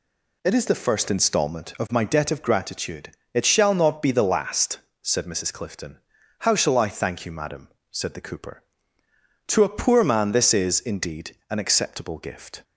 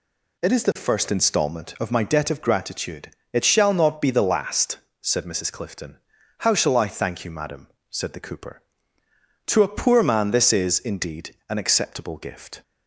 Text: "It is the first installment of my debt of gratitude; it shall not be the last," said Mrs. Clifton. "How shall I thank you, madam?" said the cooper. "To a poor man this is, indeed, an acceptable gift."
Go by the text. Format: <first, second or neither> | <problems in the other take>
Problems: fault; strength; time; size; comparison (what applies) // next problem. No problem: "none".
neither | none